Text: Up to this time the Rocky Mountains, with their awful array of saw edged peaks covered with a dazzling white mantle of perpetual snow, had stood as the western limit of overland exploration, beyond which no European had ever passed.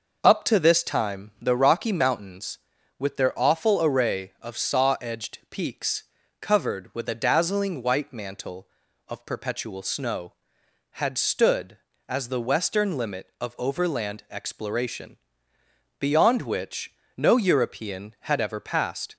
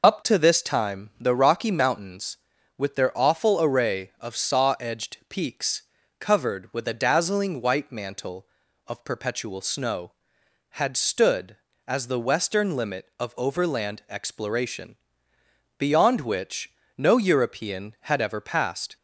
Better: first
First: pauses between "peaks" and "covered"; at 6.0 s; 0.38 s long // pauses between "which" and "no"; slight; at 16.9 s; 0.22 s long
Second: loses the start of "Up"; at 0.0 s; 35 ms // pauses between "peaks" and "covered"; at 5.8 s; 0.38 s long // pauses between "which" and "no"; slight; at 16.7 s; 0.24 s long

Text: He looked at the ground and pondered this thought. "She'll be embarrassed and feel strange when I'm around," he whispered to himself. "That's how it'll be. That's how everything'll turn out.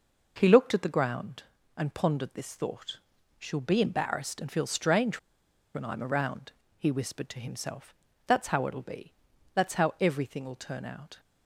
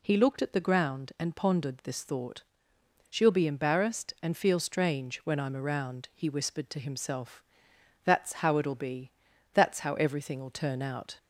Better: second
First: pauses between "strange" and "when"; noticeable; at 5.1 s; 0.55 s long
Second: none

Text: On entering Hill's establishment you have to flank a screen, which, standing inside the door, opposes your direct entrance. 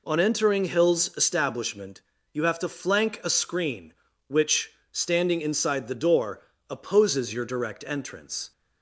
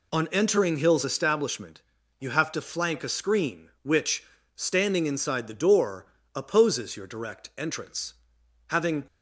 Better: first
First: pauses between "establishment" and "you"; slight; at 2.0 s; 0.32 s long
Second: pauses between "establishment" and "you"; at 1.8 s; 0.40 s long // goes on to say "Having"; slight; from 8.6 s on; 0.36 s long

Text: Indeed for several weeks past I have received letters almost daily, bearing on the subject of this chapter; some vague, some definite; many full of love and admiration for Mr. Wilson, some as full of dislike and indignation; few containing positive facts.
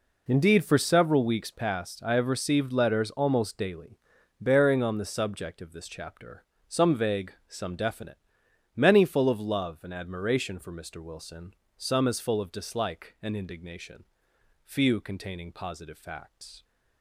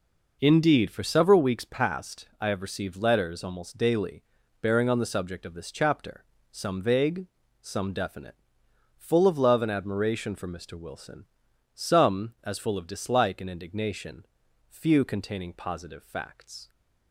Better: first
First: none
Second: skips "many"; at 8.6 s

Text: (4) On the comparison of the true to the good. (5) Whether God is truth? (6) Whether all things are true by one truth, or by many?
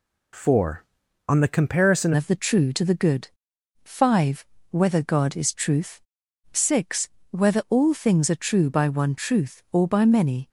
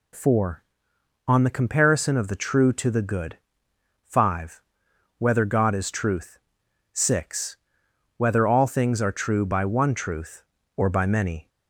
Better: second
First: changes voice at "of"; from 2.1 s on; 8.3 s long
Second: none

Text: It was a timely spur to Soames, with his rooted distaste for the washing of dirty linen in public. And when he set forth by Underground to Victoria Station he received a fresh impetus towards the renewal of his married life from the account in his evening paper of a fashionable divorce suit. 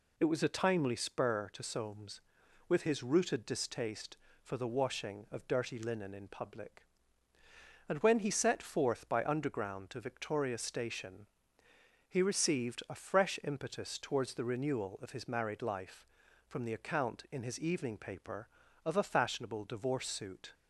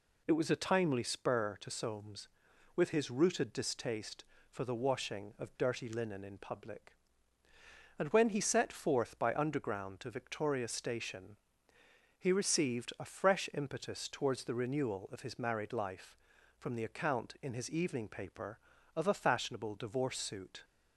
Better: neither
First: pauses between "Station" and "he"; noticeable; at 11.2 s; 0.82 s long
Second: pauses between "Station" and "he"; noticeable; at 11.3 s; 0.82 s long

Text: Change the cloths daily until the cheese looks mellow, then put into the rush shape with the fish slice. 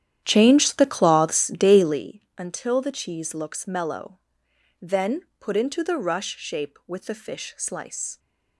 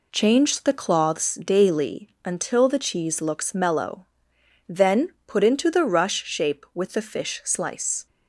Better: second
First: starts louder than the rest; strong; until 2.1 s; 11 dB // pauses between "then" and "put"; slight; at 5.2 s; 0.16 s long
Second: pauses between "then" and "put"; slight; at 5.0 s; 0.16 s long

